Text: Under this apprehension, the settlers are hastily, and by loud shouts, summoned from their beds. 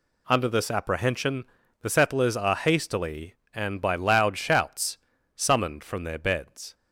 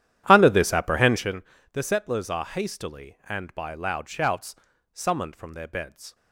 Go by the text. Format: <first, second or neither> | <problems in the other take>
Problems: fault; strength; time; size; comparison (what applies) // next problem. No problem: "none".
first | starts louder than the rest; strong; until 1.4 s; 11 dB